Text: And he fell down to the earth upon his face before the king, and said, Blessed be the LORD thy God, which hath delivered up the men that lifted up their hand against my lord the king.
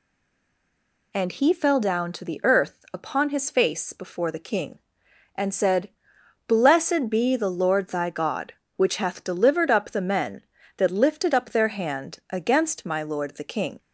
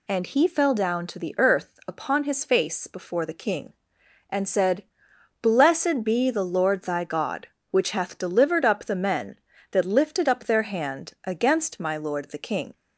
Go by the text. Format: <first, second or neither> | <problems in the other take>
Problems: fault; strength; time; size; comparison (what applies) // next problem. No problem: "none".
second | stays silent before the first word; until 1.1 s; 1.1 s long